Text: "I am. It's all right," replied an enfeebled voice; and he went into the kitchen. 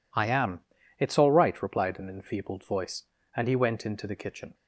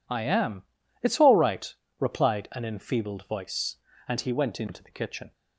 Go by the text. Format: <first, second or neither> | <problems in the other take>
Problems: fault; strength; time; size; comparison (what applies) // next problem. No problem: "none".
neither | none